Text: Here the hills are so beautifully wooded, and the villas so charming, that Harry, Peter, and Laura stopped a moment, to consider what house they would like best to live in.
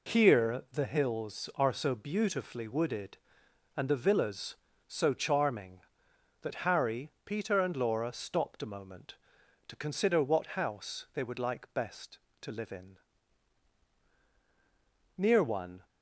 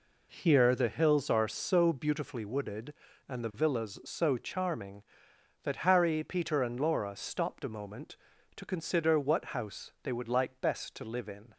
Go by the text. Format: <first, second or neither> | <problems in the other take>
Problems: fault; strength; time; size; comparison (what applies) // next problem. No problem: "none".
second | goes on to say "Near one"; noticeable; from 15.1 s on; 0.68 s long